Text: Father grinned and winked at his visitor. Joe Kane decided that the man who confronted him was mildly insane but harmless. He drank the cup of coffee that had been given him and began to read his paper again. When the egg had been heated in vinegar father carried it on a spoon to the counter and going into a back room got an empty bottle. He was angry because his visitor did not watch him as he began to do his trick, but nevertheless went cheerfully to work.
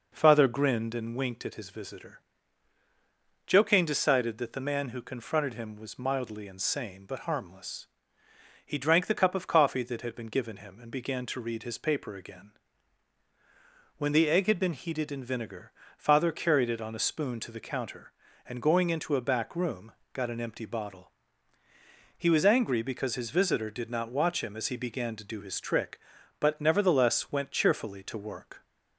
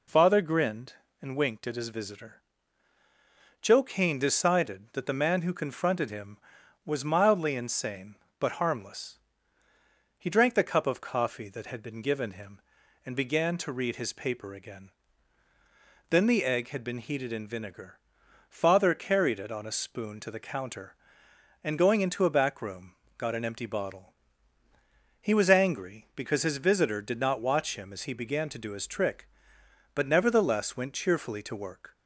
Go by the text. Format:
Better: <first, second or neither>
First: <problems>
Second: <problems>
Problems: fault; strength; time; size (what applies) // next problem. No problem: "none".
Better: first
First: pauses between "vinegar" and "father"; slight; at 15.7 s; 0.26 s long // pauses between "room" and "got"; slight; at 19.9 s; 0.22 s long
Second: says "Then" for "When"; at 16.0 s // pauses between "vinegar" and "father"; noticeable; at 17.9 s; 0.50 s long // pauses between "room" and "got"; slight; at 22.9 s; 0.26 s long